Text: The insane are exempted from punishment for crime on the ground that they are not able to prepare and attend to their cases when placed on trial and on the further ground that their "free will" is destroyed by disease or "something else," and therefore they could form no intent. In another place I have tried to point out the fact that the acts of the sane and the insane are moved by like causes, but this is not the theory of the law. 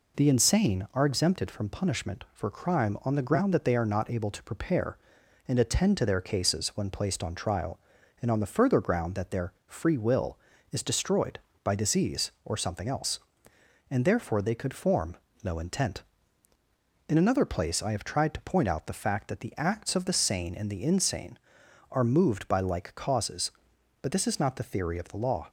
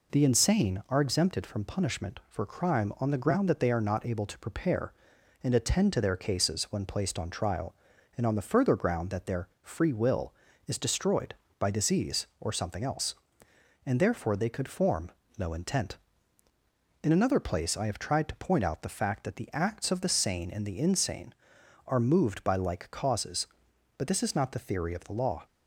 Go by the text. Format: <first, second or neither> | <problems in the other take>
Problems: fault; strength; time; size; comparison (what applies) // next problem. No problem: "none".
neither | pauses between "their" and "free"; slight; the same in both // pauses between "form" and "no"; slight; the same in both